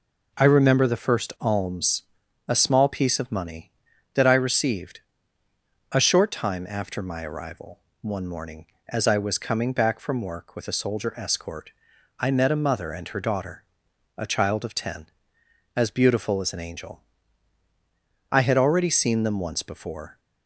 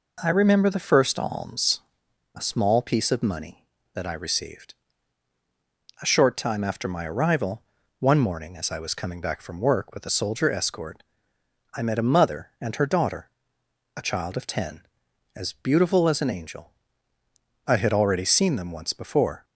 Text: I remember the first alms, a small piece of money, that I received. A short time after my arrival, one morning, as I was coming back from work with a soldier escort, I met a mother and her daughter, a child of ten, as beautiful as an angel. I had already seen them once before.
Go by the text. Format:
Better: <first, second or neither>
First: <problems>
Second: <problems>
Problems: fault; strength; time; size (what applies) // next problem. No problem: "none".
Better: neither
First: none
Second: none